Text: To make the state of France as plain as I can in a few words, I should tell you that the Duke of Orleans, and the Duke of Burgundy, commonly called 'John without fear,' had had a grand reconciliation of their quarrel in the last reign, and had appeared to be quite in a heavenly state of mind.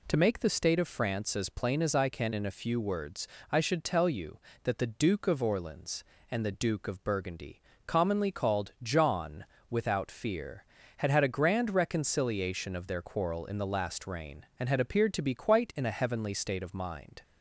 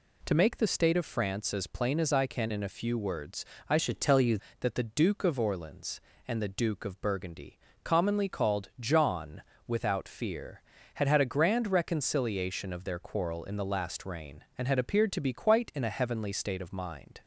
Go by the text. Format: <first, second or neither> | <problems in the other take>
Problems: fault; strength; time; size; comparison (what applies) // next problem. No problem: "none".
first | changes voice from "should" to "you"; from 3.7 to 4.3 s; 0.6 s long // pauses between "John" and "without"; slight; at 9.4 s; 0.24 s long; slight in the first